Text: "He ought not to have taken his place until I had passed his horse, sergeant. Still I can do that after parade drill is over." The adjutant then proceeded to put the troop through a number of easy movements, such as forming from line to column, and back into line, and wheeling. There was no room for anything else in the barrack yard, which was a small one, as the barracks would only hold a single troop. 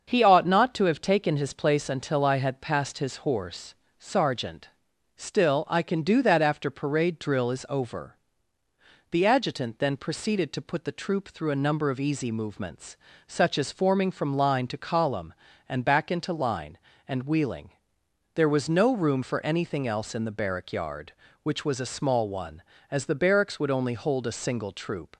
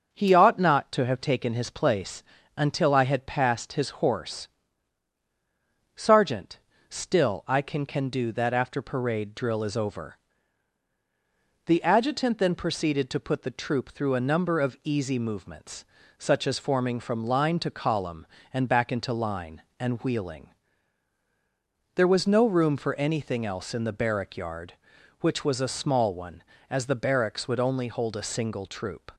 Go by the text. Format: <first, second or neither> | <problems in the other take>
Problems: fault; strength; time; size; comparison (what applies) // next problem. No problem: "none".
first | starts louder than the rest; until 1.1 s; 7 dB; also in the first // pauses between "place" and "until"; slight; at 2.2 s; 0.34 s long // says "can" twice; at 7.8 s